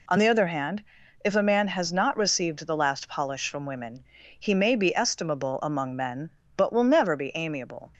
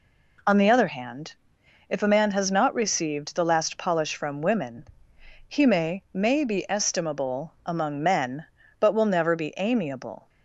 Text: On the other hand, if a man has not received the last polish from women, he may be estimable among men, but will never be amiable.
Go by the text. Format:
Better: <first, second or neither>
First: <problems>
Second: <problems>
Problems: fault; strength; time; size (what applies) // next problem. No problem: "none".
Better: first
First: none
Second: says "may" twice; at 6.1 s